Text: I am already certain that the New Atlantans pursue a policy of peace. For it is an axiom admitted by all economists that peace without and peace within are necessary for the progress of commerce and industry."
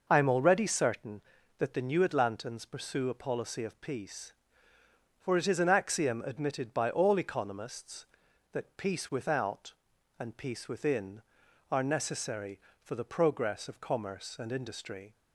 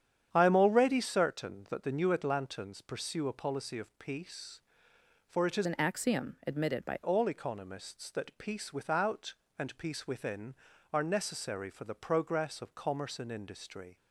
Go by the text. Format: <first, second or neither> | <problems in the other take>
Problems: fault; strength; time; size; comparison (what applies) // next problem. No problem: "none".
first | starts louder than the rest; strong; until 1.3 s; 9 dB // changes voice from "an" to "by"; from 5.6 to 6.9 s; 1.3 s long